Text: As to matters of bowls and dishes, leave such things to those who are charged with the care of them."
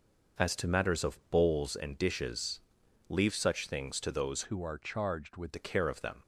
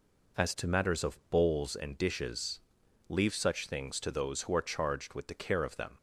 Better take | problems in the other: second | starts louder than the rest; noticeable; until 1.5 s; 6 dB // changes voice from "who" to "with"; from 4.4 to 5.5 s; 1.1 s long

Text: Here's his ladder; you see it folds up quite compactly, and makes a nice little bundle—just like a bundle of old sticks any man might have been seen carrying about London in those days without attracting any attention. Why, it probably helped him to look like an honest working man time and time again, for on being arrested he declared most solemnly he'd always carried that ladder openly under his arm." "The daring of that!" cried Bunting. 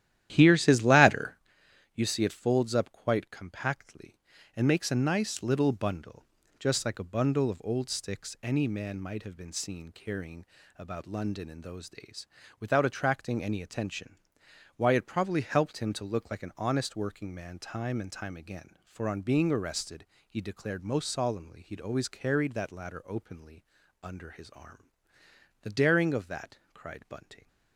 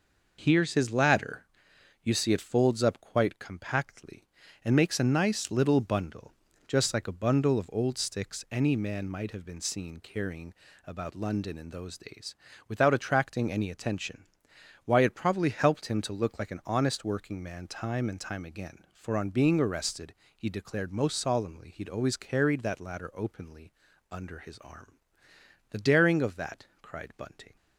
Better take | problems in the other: second | starts louder than the rest; strong; until 1.5 s; 12 dB // pauses between "carrying" and "about"; slight; at 10.4 s; 0.34 s long; slight in the second // pauses between "days" and "without"; slight; at 12.2 s; 0.34 s long; slight in the second // pauses between "arrested" and "he"; slight; at 20.0 s; 0.24 s long; slight in the second // pauses between "openly" and "under"; slight; at 23.6 s; 0.36 s long; slight in the second

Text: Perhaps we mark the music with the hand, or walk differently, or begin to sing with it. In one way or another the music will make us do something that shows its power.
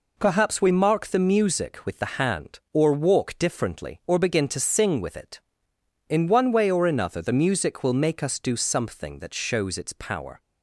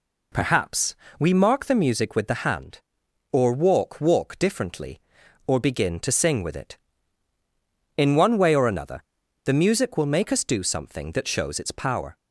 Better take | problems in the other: first | pauses between "Perhaps" and "we"; slight; at 0.9 s; 0.24 s long // says "walk" twice; at 4.0 s // pauses between "another" and "the"; at 9.0 s; 0.42 s long

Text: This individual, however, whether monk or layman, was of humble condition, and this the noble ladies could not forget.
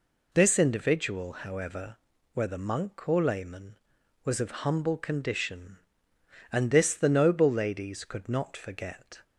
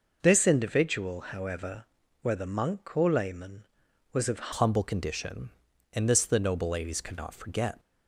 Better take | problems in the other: first | changes voice at "humble"; from 4.5 s on; 3.2 s long

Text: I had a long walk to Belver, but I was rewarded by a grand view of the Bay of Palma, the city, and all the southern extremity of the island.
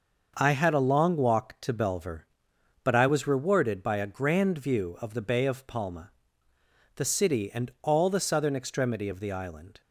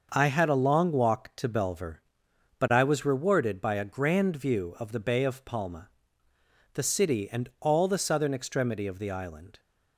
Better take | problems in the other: neither | starts louder than the rest; the same in both

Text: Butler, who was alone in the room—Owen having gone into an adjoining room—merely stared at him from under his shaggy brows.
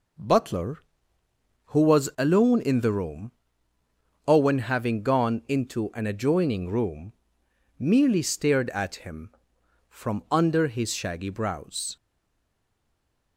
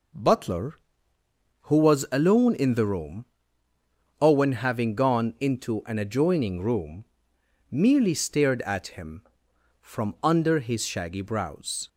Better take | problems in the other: second | stays silent after the last word; noticeable; from 11.9 s on; 1.4 s long

